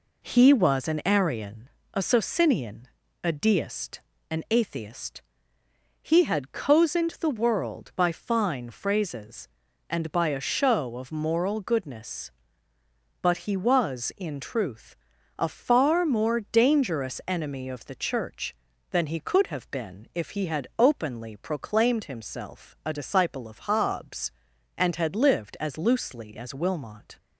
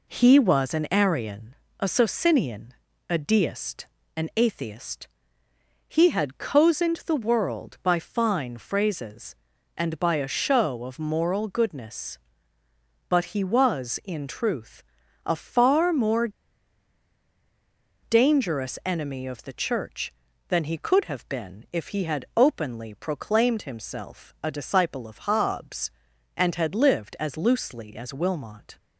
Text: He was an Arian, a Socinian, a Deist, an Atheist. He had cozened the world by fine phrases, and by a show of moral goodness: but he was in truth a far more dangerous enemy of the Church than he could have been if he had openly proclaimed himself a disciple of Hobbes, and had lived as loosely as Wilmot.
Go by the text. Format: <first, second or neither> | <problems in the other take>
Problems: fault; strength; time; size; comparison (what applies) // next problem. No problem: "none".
first | pauses between "truth" and "a"; at 14.8 s; 0.44 s long; also in the first // pauses between "more" and "dangerous"; strong; at 16.2 s; 1.7 s long